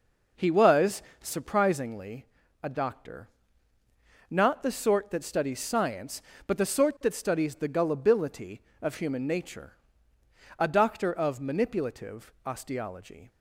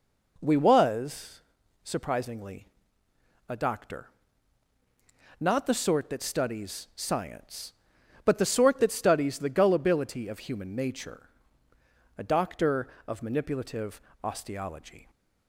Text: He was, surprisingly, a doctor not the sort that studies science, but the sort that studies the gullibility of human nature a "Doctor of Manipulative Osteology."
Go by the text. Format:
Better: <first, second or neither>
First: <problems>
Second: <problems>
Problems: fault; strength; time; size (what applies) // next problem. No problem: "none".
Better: first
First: pauses between "doctor" and "not"; at 3.2 s; 1.0 s long // pauses between "nature" and "a"; noticeable; at 9.7 s; 0.84 s long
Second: says "We" for "He"; at 0.4 s // pauses between "doctor" and "not"; strong; at 4.0 s; 1.3 s long // pauses between "nature" and "a"; noticeable; at 11.2 s; 0.88 s long // pauses between "Manipulative" and "Osteology"; slight; at 14.0 s; 0.20 s long